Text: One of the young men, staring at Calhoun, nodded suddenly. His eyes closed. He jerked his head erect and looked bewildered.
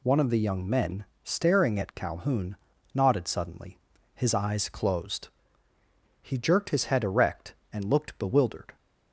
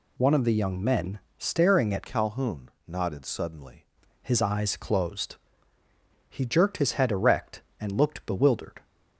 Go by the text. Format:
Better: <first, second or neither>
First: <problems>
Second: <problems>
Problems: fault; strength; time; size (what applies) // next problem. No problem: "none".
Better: first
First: none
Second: changes voice from "Calhoun" to "suddenly"; from 2.0 to 3.8 s; 1.8 s long